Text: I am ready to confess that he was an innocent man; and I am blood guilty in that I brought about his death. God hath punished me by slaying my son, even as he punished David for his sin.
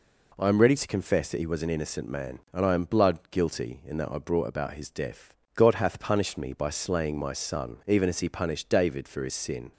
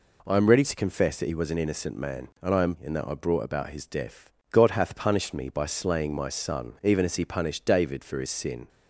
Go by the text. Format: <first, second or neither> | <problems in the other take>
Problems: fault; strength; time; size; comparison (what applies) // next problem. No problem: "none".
first | skips "blood guilty"; at 2.7 s